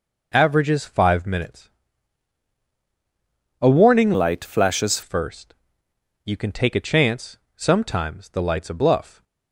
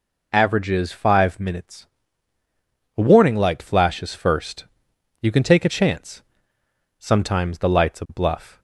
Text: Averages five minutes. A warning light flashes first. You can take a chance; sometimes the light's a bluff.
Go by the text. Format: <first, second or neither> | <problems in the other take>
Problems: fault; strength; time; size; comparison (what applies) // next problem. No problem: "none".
second | changes voice from "light" to "flashes"; from 4.1 to 5.0 s; 0.9 s long